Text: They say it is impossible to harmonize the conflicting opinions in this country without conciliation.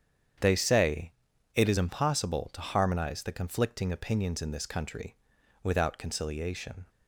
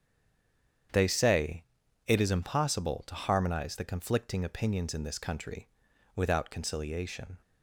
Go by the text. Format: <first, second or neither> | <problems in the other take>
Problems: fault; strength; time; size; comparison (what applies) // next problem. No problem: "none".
first | stays silent before the first word; slight; until 0.8 s; 0.8 s long // starts louder than the rest; strong; until 2.3 s; 8.5 dB; strong in the first // pauses between "say" and "it"; noticeable; at 1.6 s; 0.46 s long; noticeable in the first // pauses between "country" and "without"; noticeable; at 5.6 s; 0.48 s long; noticeable in the first